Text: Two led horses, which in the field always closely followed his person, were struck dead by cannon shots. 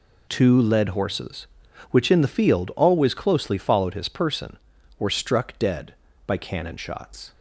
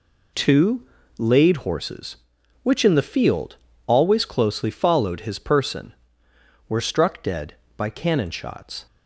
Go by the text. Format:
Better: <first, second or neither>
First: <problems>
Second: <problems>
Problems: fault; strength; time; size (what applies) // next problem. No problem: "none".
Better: first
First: none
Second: says "laid" for "led"; at 1.1 s // pauses between "field" and "always"; slight; at 3.5 s; 0.30 s long